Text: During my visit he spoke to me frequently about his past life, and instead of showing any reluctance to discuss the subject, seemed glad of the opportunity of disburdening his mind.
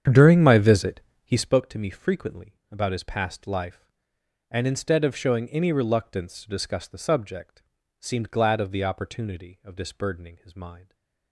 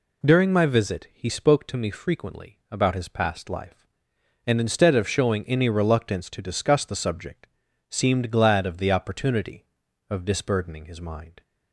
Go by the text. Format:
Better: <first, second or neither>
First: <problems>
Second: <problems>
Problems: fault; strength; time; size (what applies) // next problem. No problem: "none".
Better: second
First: starts louder than the rest; strong; until 1.6 s; 8.5 dB // pauses between "visit" and "he"; slight; at 1.0 s; 0.24 s long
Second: none